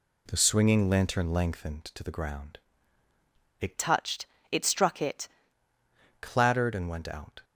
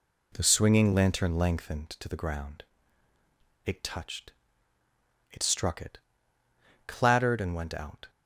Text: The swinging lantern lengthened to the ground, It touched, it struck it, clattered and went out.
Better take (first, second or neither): second